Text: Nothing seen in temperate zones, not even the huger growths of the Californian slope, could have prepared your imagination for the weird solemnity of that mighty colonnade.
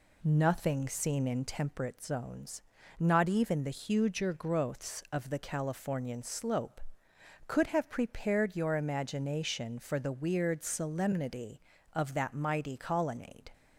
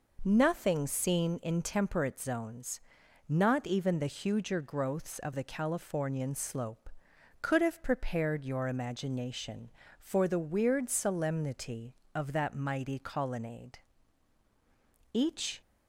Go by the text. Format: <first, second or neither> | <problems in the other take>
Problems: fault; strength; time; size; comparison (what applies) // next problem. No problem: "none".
first | goes on to say "Each"; slight; from 15.1 s on; 0.48 s long